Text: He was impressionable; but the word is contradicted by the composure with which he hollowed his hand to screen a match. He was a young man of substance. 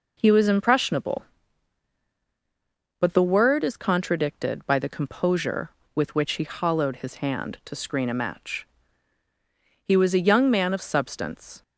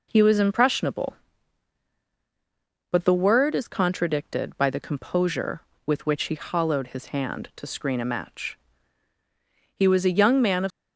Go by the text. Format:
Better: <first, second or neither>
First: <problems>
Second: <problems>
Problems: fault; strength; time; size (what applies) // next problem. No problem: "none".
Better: first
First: none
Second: stops before "substance"; at 10.7 s